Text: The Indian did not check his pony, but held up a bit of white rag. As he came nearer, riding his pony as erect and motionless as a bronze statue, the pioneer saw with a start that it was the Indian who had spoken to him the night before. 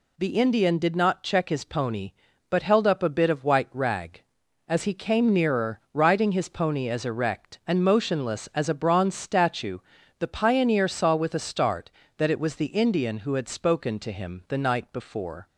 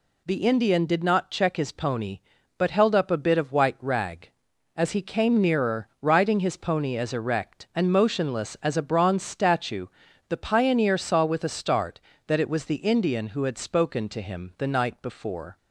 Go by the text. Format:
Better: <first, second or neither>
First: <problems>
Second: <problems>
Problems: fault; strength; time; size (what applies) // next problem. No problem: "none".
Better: neither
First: none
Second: none